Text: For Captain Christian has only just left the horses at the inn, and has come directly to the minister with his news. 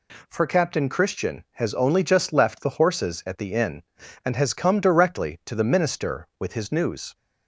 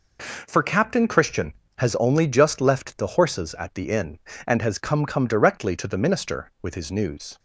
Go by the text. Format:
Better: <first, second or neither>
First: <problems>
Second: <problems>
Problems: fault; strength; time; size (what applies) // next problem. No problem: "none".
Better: first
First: none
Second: says "come" twice; at 5.0 s